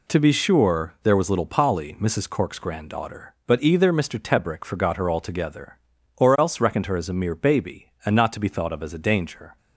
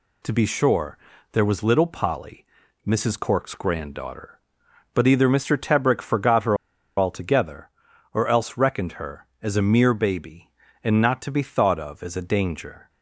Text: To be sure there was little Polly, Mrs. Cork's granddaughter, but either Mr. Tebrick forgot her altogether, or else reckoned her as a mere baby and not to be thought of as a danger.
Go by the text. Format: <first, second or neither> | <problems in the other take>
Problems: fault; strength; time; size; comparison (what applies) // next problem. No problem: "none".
first | pauses between "sure" and "there"; slight; at 0.9 s; 0.34 s long // pauses between "her" and "altogether"; at 6.5 s; 0.42 s long